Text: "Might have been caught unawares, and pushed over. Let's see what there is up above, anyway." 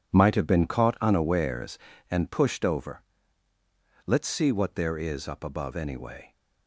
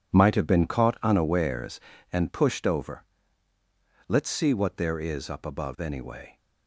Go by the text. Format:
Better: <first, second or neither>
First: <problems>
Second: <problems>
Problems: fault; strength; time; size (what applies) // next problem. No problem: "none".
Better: neither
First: none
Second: none